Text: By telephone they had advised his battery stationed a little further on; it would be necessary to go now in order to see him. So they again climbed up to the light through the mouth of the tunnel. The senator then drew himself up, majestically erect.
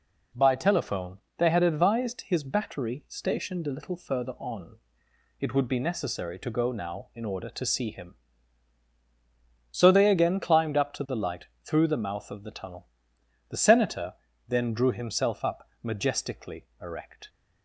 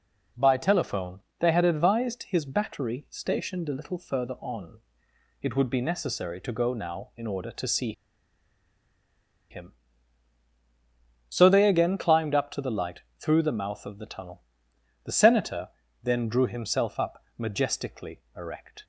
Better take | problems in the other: first | pauses between "telephone" and "they"; slight; at 1.1 s; 0.18 s long; slight in the first // pauses between "see" and "him"; strong; at 7.9 s; 1.5 s long // pauses between "light" and "through"; slight; at 13.0 s; 0.16 s long; slight in the first // pauses between "senator" and "then"; slight; at 15.6 s; 0.34 s long; slight in the first

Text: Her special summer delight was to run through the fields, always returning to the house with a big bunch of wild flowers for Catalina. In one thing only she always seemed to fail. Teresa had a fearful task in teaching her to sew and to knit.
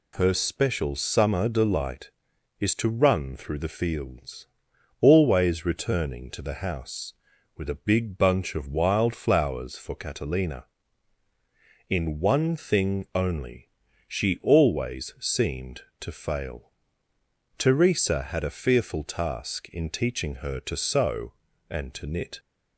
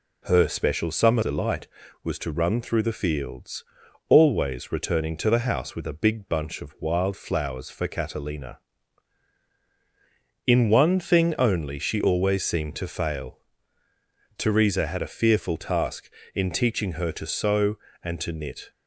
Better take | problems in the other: second | says "is" for "was"; at 2.6 s // pauses between "only" and "she"; slight; at 13.7 s; 0.36 s long

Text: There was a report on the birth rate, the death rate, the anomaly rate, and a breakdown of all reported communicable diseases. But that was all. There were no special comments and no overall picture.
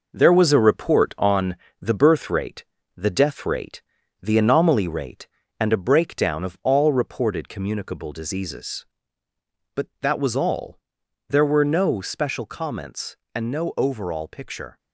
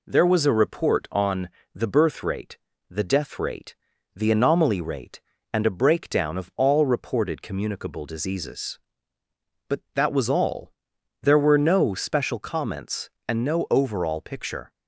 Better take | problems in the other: second | gets quieter; throughout; 6 dB // pauses between "on" and "the"; slight; at 1.5 s; 0.26 s long; slight in the second

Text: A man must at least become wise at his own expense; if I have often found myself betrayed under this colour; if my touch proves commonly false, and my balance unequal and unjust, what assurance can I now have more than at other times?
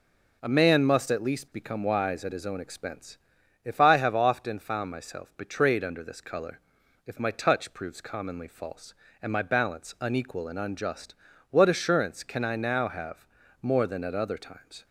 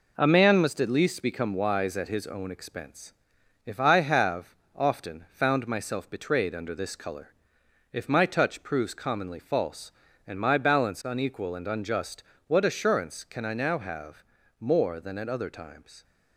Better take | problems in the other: first | gets quieter; noticeable; throughout; 5.5 dB // pauses between "have" and "often"; slight; at 4.5 s; 0.18 s long // pauses between "have" and "more"; slight; at 14.2 s; 0.36 s long; slight in the first

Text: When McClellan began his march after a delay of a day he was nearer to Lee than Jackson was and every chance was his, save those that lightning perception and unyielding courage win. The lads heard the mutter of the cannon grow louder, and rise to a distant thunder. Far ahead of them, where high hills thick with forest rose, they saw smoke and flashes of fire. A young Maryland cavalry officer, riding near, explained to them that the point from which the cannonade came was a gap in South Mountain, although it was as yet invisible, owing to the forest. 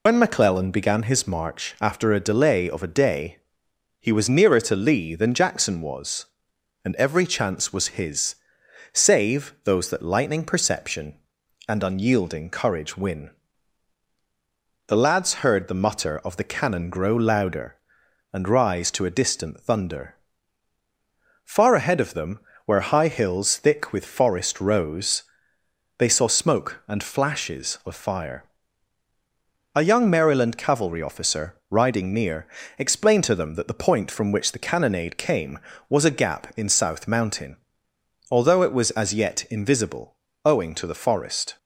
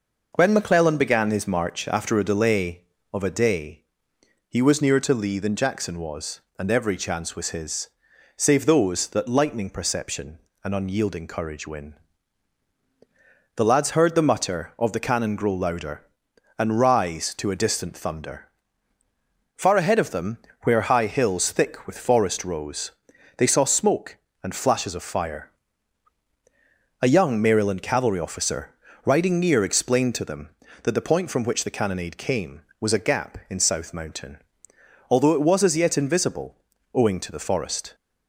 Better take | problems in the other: second | loses the start of "When"; at 0.0 s; 60 ms // pauses between "day" and "he"; noticeable; at 3.3 s; 0.62 s long; noticeable in the second

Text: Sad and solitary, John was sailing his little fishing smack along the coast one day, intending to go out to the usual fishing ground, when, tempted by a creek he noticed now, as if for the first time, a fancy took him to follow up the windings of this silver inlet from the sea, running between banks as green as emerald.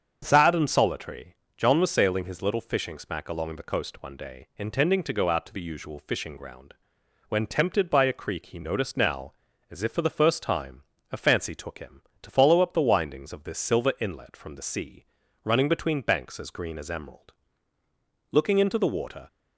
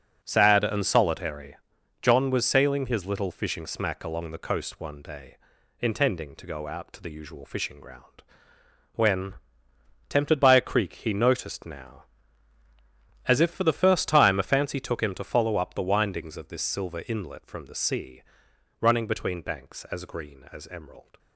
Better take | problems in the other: second | starts louder than the rest; until 1.2 s; 7 dB; also in the second // goes on to say "Looking into the water"; noticeable; from 18.3 s on; 0.96 s long

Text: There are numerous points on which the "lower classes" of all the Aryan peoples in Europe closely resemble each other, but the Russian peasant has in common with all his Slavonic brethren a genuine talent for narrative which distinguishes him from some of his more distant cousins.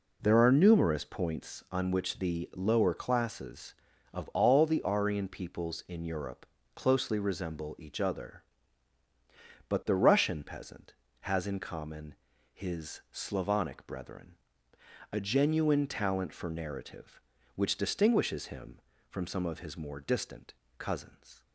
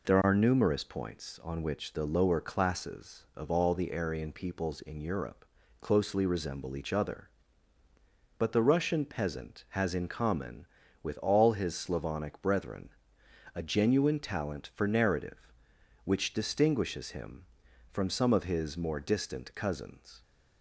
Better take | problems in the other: second | pauses between "Europe" and "closely"; slight; at 6.4 s; 0.30 s long; also in the second // skips "with all"; at 12.3 s // pauses between "brethren" and "a"; noticeable; at 14.3 s; 0.76 s long; noticeable in the second // pauses between "distant" and "cousins"; slight; at 20.5 s; 0.24 s long

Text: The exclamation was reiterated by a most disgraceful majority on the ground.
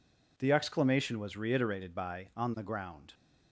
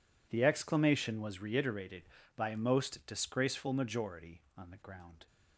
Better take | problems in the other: second | skips "a most disgraceful majority"; at 2.3 s

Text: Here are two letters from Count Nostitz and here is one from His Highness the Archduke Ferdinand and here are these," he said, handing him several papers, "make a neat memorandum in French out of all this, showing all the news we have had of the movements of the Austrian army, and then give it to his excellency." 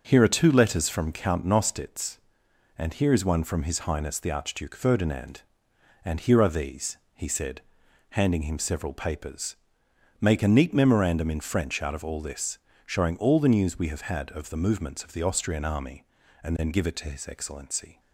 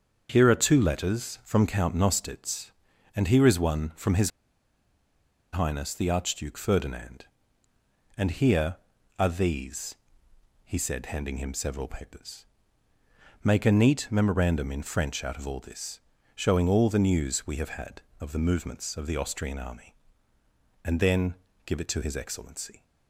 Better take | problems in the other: first | starts louder than the rest; until 1.3 s; 7 dB // pauses between "His" and "Highness"; at 4.3 s; 1.2 s long // pauses between "then" and "give"; slight; at 21.3 s; 0.32 s long

